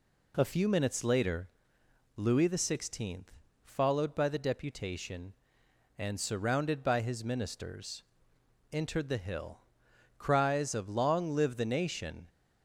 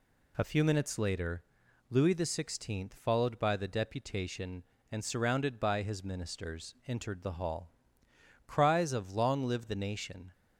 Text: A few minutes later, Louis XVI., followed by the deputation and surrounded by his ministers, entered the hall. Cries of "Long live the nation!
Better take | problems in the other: second | says "hill" for "hall"; at 9.1 s

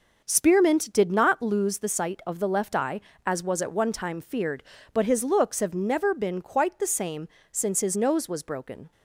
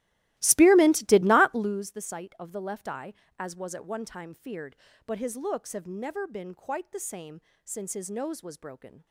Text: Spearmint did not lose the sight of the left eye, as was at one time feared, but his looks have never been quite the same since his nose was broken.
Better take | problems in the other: first | starts louder than the rest; strong; until 1.8 s; 16.5 dB // pauses between "same" and "since"; slight; at 7.3 s; 0.24 s long; slight in the first

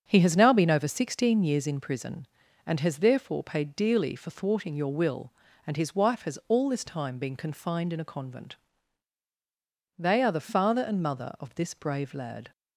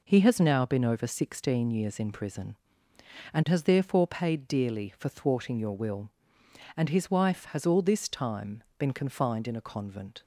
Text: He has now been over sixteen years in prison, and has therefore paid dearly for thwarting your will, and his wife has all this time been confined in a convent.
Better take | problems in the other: second | starts louder than the rest; strong; until 1.0 s; 7.5 dB // goes on to say "They are the father and mother of this brave lad"; strong; from 9.9 s on; 2.5 s long

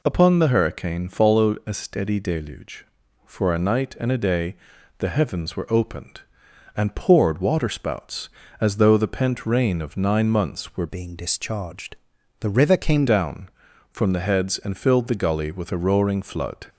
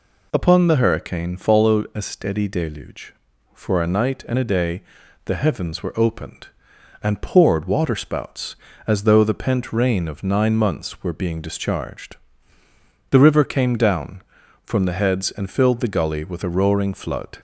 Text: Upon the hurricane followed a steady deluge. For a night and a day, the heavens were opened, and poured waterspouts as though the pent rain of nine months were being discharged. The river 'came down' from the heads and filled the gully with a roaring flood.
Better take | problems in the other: second | changes voice from "being" to "came"; from 10.8 to 13.0 s; 2.2 s long

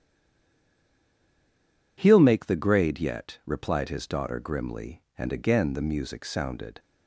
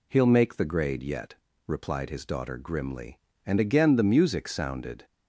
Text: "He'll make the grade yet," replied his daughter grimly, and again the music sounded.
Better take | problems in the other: second | stays silent before the first word; noticeable; until 1.9 s; 1.9 s long

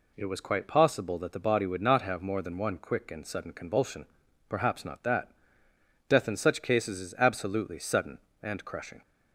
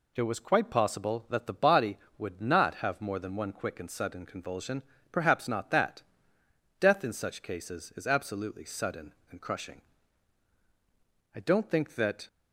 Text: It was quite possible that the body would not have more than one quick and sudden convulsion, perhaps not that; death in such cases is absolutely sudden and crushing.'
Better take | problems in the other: first | goes on to say "I don't think that"; noticeable; from 11.3 s on; 0.94 s long

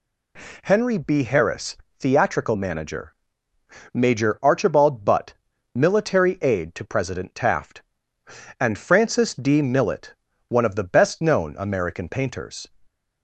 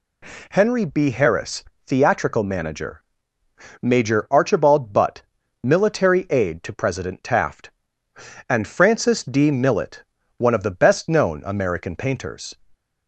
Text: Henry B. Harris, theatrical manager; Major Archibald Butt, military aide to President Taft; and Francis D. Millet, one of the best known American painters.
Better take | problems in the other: neither | none

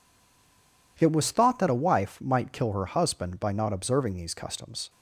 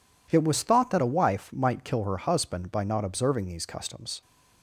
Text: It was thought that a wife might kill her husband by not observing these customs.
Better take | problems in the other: second | stays silent before the first word; slight; until 0.9 s; 0.9 s long

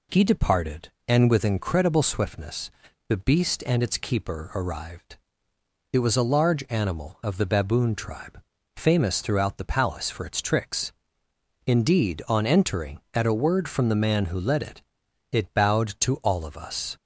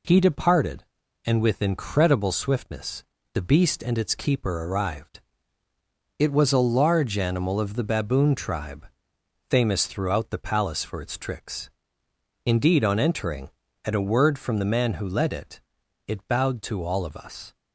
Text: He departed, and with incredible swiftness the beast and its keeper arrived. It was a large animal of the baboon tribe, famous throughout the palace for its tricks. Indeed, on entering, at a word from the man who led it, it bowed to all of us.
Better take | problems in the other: neither | pauses between "swiftness" and "the"; slight; the same in both

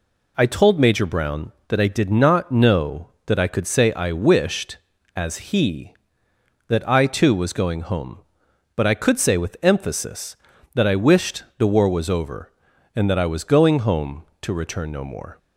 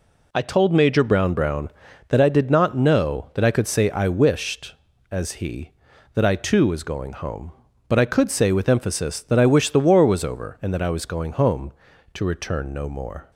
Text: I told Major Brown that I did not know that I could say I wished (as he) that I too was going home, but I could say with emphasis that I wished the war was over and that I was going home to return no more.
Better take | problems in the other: first | says "Brown" twice; at 1.3 s

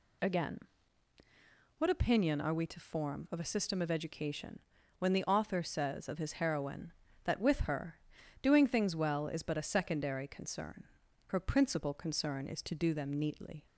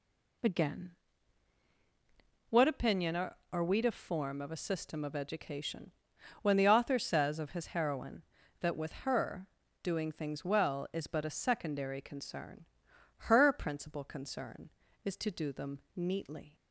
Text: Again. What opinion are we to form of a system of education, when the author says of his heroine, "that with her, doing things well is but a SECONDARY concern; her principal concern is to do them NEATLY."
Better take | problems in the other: first | says "are" twice; at 3.5 s

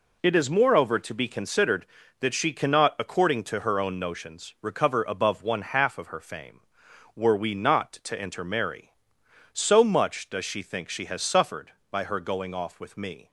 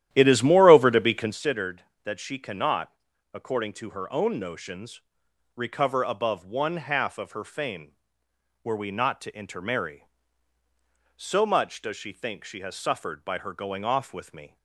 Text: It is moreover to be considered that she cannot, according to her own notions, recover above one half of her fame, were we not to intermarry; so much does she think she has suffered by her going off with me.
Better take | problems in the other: first | starts louder than the rest; strong; until 1.4 s; 12 dB

